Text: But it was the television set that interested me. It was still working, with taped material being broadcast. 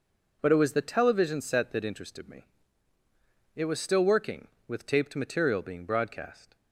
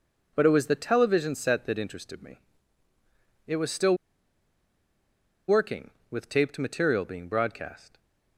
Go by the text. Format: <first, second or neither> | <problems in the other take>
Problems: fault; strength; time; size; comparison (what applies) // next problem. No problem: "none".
first | pauses between "still" and "working"; strong; at 3.9 s; 1.5 s long